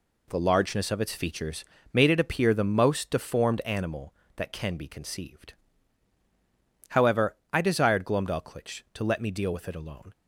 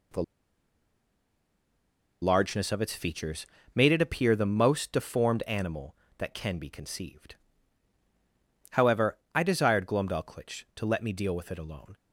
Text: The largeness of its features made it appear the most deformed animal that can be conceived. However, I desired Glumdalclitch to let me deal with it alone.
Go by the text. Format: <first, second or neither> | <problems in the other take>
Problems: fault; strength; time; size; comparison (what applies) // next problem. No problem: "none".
first | pauses between "The" and "largeness"; strong; at 0.2 s; 1.9 s long // pauses between "features" and "made"; slight; at 3.4 s; 0.30 s long; slight in the first